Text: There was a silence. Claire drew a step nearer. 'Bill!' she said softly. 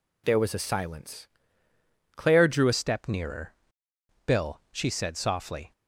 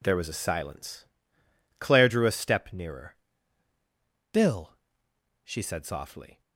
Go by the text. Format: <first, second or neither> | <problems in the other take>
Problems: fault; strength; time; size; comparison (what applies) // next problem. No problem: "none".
second | changes voice at "step"; from 2.7 s on; 3.0 s long